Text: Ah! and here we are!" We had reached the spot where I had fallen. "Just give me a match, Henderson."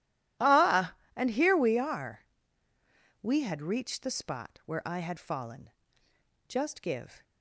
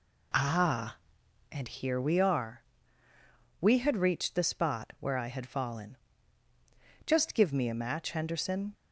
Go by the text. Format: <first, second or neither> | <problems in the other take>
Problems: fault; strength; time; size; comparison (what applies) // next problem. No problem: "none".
second | stops before "me a match Henderson"; at 7.2 s